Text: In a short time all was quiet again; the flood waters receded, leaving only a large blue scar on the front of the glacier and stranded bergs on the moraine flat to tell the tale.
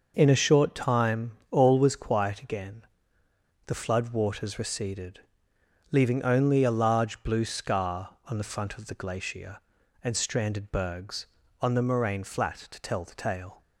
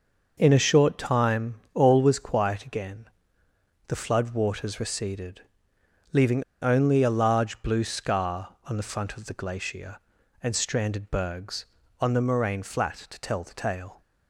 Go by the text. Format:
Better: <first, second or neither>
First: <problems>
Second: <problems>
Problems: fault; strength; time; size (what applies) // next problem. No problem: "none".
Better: first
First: pauses between "time" and "all"; slight; at 1.3 s; 0.20 s long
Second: pauses between "time" and "all"; slight; at 1.5 s; 0.20 s long // pauses between "leaving" and "only"; slight; at 6.4 s; 0.18 s long